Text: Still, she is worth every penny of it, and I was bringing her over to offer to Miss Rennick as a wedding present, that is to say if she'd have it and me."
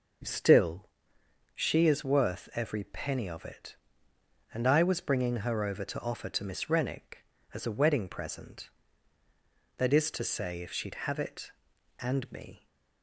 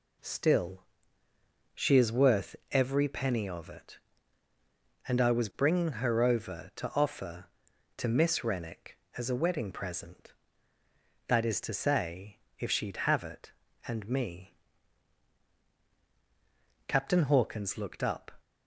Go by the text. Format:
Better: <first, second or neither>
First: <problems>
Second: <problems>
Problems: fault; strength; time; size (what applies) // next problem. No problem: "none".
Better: first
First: none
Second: pauses between "worth" and "every"; slight; at 2.5 s; 0.16 s long // pauses between "say" and "if"; slight; at 12.3 s; 0.22 s long // goes on to say "Captain Hawkins looked up"; from 16.8 s on; 1.4 s long